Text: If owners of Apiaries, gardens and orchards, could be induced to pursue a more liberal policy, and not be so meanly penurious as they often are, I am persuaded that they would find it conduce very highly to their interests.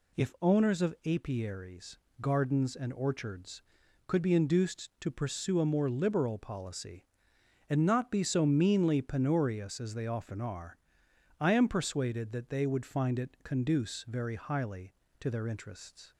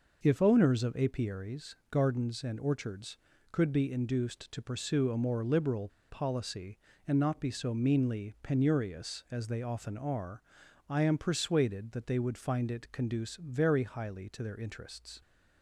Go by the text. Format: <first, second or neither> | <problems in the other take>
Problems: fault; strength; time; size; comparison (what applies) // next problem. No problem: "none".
first | pauses between "liberal" and "policy"; slight; at 5.8 s; 0.21 s long